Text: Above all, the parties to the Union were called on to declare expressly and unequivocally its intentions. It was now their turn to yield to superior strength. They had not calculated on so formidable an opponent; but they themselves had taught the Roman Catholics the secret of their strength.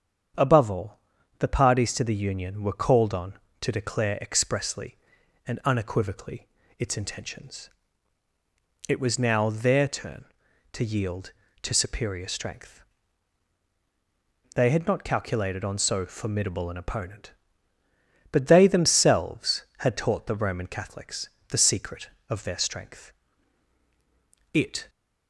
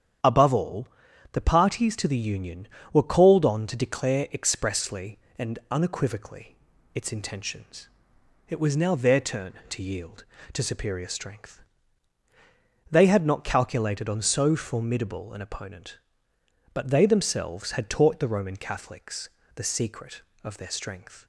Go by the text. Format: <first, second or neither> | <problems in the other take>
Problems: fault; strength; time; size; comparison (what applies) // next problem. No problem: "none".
second | starts louder than the rest; strong; until 1.7 s; 8 dB; strong in the second // pauses between "unequivocally" and "its"; slight; at 6.4 s; 0.30 s long; slight in the second // pauses between "Catholics" and "the"; slight; at 21.2 s; 0.18 s long; slight in the second // goes on to say "It"; slight; from 24.5 s on; 0.36 s long